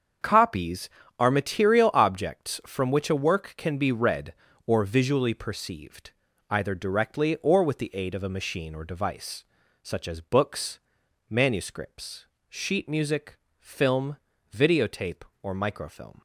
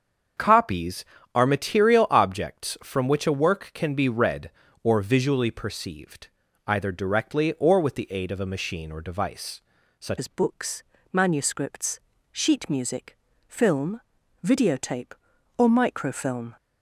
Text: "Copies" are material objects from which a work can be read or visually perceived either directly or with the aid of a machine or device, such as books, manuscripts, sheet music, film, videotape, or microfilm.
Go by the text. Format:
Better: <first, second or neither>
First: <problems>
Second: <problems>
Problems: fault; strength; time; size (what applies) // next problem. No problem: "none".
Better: first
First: starts louder than the rest; until 1.5 s; 7 dB // pauses between "perceived" and "either"; at 6.1 s; 0.38 s long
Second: starts louder than the rest; until 1.6 s; 7 dB // pauses between "perceived" and "either"; at 6.2 s; 0.38 s long // changes voice at "as"; from 10.1 s on; 6.4 s long